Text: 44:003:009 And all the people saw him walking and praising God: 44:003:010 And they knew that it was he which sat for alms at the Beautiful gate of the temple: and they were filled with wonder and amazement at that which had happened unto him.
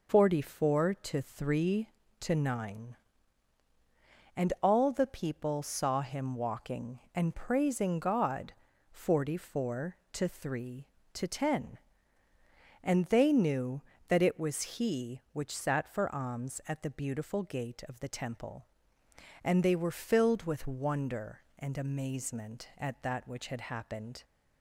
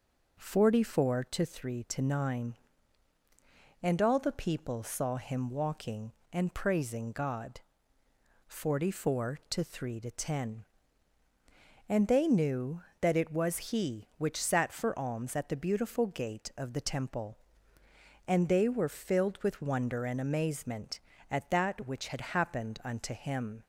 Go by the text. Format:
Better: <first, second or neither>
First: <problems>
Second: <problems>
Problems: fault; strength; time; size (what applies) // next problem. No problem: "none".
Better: second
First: stops before "unto him"; at 24.2 s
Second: none